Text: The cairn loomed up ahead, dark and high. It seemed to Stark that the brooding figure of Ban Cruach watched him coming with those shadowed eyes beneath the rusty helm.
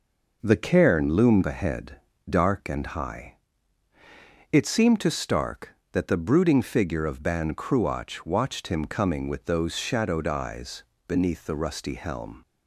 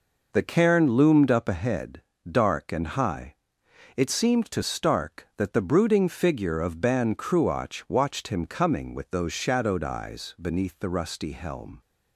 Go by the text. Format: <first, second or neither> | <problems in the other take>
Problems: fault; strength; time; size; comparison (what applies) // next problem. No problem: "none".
second | skips "up"; at 1.4 s // pauses between "eyes" and "beneath"; slight; at 10.8 s; 0.24 s long